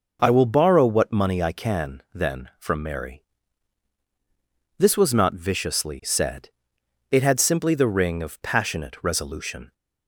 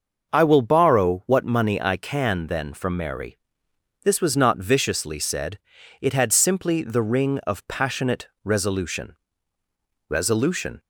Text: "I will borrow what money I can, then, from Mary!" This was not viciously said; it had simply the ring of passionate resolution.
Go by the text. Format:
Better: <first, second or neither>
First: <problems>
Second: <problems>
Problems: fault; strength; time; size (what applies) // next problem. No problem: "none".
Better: first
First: none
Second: starts louder than the rest; noticeable; until 1.3 s; 6 dB // pauses between "passionate" and "resolution"; slight; at 8.2 s; 0.16 s long // says "resolution" twice; at 10.0 s